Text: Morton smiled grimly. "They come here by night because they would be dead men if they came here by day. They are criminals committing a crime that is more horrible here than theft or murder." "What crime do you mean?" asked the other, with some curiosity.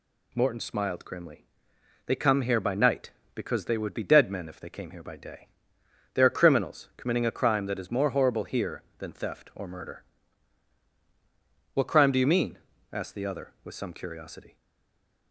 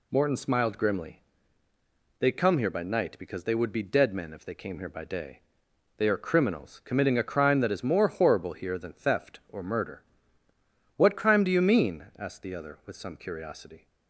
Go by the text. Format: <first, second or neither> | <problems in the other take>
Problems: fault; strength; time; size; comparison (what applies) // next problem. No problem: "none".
second | stays silent after the last word; slight; from 14.5 s on; 0.8 s long